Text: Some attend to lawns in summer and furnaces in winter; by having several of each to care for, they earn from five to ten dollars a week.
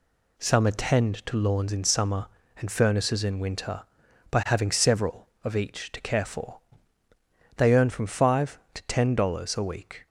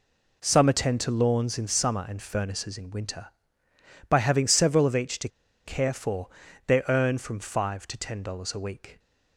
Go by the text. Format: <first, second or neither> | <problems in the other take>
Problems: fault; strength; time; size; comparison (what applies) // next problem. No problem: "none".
first | pauses between "to" and "care"; at 5.2 s; 0.37 s long